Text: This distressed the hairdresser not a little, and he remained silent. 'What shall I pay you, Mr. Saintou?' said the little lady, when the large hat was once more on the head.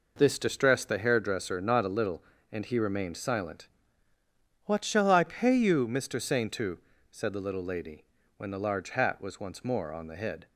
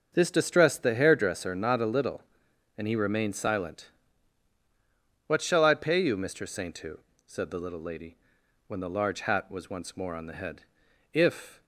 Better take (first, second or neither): first